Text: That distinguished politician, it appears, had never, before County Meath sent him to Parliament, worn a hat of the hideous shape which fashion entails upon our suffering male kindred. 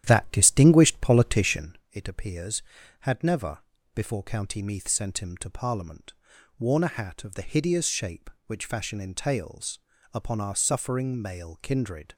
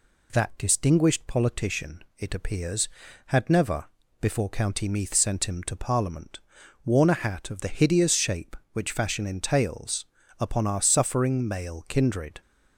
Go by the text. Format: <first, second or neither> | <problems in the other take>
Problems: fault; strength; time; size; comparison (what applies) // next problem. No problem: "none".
second | starts louder than the rest; strong; until 1.8 s; 11 dB // pauses between "entails" and "upon"; slight; at 9.7 s; 0.34 s long; slight in the second